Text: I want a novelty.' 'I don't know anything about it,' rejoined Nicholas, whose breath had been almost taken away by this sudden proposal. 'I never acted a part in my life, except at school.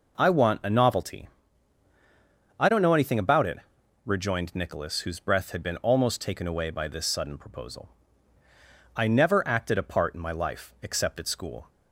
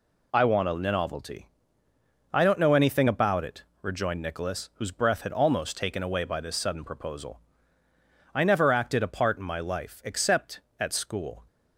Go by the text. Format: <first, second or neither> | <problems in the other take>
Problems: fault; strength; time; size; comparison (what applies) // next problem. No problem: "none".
first | skips "been"; at 5.3 s